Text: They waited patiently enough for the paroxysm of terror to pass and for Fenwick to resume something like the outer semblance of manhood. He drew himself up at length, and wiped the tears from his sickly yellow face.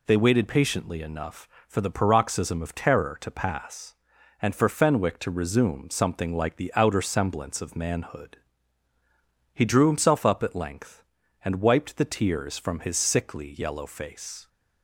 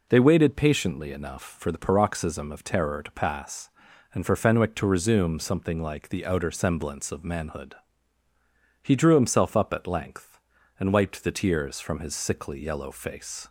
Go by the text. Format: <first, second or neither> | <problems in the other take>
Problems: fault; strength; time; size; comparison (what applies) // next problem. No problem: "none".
neither | none